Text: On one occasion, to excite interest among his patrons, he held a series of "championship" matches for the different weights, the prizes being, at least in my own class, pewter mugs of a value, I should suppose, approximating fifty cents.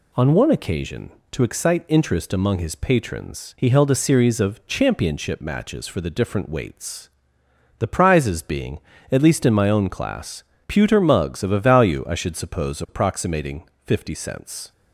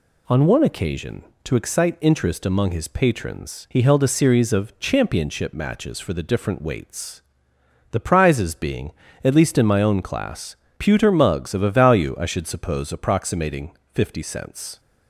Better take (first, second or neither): neither